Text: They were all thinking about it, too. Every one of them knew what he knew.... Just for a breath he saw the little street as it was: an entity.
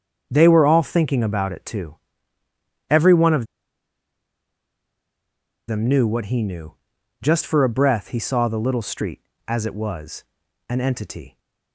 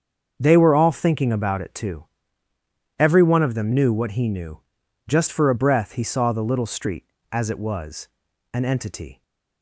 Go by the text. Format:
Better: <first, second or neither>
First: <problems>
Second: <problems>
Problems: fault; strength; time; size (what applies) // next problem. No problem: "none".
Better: second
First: starts louder than the rest; until 1.3 s; 7 dB // pauses between "of" and "them"; strong; at 3.4 s; 2.2 s long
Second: starts louder than the rest; until 1.3 s; 7 dB